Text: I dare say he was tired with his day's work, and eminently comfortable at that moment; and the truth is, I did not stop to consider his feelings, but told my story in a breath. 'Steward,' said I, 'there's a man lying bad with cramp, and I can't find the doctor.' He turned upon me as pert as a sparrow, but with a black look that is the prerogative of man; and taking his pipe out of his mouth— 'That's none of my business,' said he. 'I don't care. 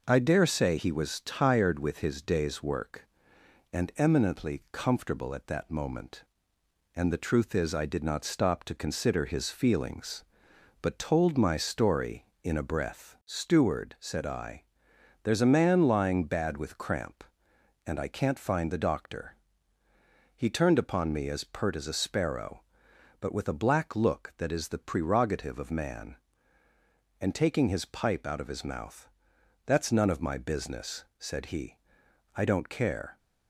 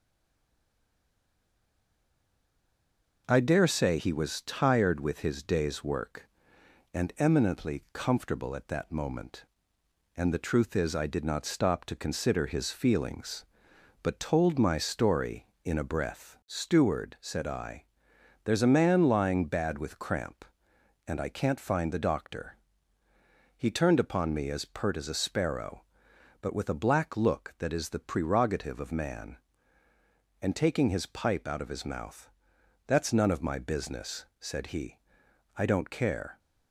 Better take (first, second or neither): first